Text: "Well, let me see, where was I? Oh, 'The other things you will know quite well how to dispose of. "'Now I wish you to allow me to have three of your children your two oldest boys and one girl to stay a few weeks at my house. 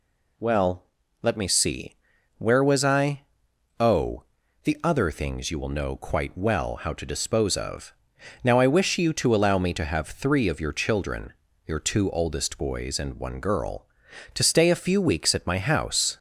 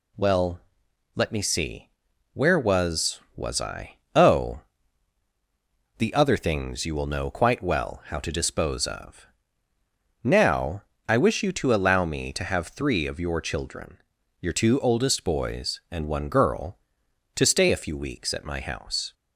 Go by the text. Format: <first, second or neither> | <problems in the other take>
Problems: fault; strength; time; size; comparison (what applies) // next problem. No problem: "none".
first | says "was" twice; at 3.3 s // pauses between "Now" and "I"; slight; at 10.8 s; 0.24 s long // pauses between "children" and "your"; at 13.9 s; 0.42 s long; slight in the first